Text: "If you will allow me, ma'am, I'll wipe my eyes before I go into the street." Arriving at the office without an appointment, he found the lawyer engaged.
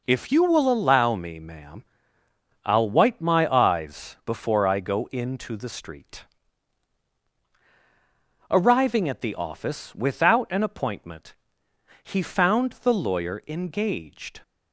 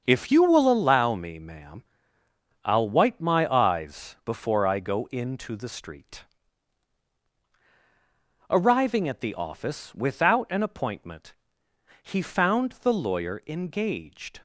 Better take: first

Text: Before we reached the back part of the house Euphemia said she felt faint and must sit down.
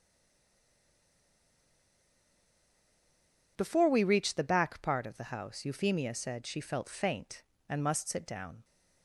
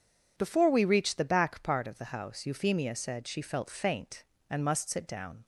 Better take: second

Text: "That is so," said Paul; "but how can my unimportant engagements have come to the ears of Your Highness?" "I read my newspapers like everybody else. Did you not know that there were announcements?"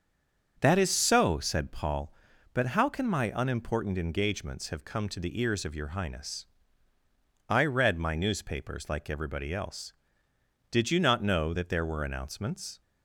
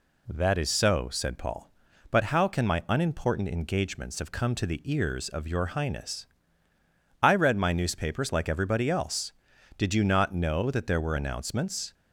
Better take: second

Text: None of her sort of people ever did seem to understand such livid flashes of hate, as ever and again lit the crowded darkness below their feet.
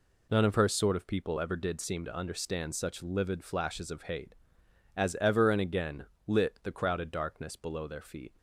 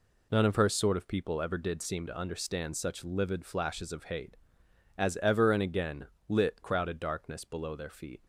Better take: first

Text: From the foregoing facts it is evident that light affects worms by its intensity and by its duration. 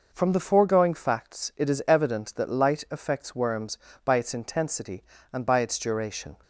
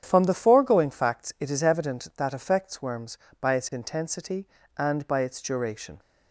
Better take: first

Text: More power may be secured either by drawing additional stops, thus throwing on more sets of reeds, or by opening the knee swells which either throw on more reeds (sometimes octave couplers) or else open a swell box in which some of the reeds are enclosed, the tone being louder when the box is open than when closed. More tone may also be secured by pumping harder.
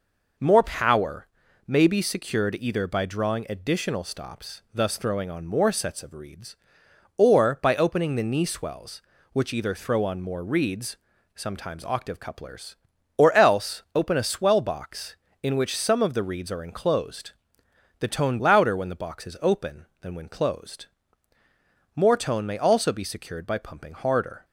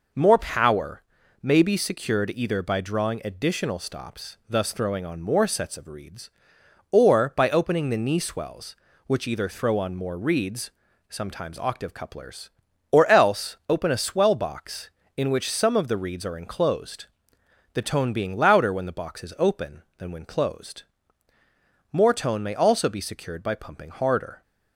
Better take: second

